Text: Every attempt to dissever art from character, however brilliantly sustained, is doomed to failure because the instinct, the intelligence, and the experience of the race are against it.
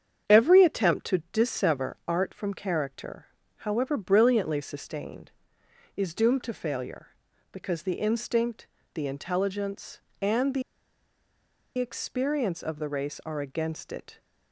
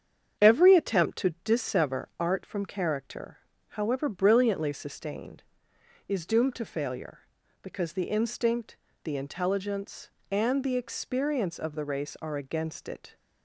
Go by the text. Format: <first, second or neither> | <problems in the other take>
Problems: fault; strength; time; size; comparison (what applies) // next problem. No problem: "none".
second | starts louder than the rest; strong; until 1.4 s; 8 dB; strong in the second // pauses between "the" and "experience"; at 10.6 s; 1.1 s long